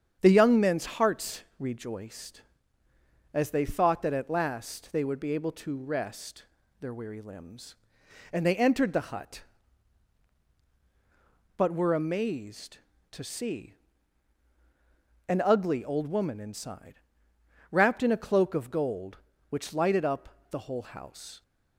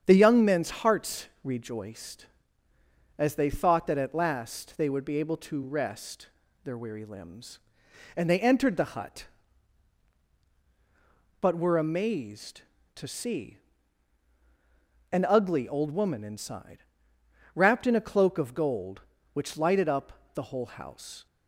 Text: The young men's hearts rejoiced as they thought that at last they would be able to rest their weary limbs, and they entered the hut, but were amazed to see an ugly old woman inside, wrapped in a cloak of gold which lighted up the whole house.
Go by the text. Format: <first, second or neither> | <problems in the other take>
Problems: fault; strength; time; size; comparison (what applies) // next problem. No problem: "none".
neither | starts louder than the rest; strong; the same in both // pauses between "hearts" and "rejoiced"; slight; the same in both // pauses between "rest" and "their"; slight; the same in both // pauses between "see" and "an"; strong; the same in both